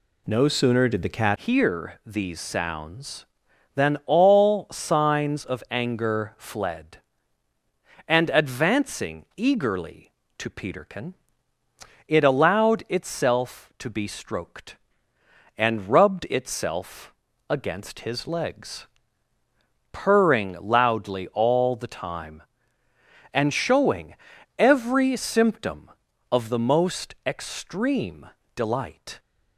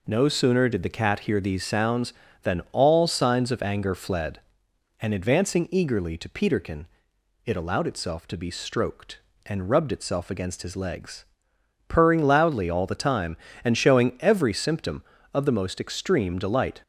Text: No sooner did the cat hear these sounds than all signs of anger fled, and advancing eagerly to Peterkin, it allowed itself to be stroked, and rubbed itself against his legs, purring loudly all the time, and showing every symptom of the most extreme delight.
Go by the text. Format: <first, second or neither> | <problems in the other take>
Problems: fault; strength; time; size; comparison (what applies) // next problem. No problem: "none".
second | changes voice at "hear"; from 1.3 s on; 27.8 s long // pauses between "itself" and "against"; slight; at 17.1 s; 0.36 s long // pauses between "showing" and "every"; at 24.1 s; 0.44 s long // pauses between "extreme" and "delight"; slight; at 28.2 s; 0.26 s long